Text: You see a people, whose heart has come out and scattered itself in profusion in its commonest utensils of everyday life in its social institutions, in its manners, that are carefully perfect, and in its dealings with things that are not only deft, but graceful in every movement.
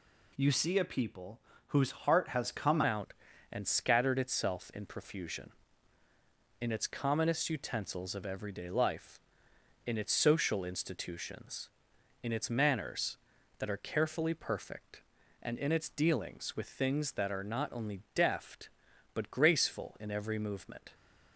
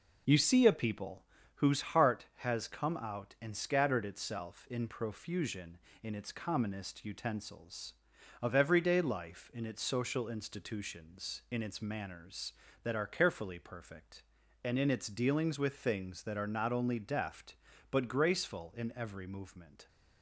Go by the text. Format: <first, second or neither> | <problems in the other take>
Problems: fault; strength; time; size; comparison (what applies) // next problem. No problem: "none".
second | changes voice at "out"; from 2.8 s on; 18.0 s long